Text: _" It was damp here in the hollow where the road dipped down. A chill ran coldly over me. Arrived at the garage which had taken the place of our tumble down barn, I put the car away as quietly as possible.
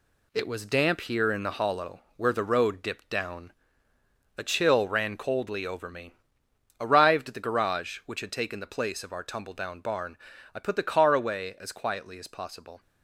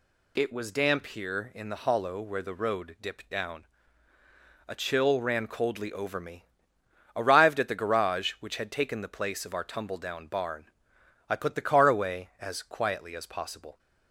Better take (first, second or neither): second